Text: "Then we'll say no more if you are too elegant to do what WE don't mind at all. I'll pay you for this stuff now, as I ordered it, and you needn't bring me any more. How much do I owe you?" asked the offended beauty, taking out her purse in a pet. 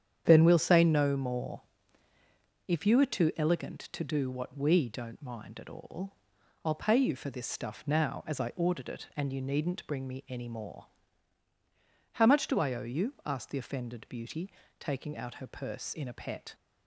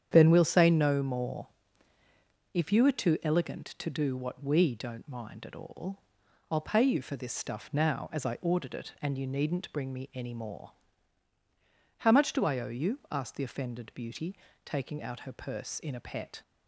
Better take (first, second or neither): neither